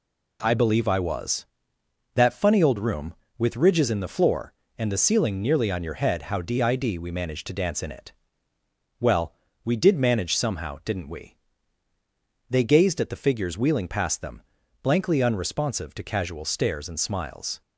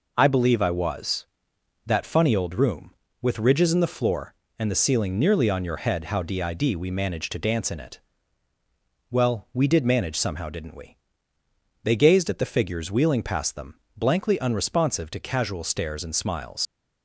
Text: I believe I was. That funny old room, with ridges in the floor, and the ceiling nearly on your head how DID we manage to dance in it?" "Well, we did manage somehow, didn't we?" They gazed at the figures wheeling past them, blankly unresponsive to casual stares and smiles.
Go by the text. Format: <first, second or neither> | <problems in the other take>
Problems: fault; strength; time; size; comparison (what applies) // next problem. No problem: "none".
first | leaves "smiles" unfinished; at 16.6 s; 105 ms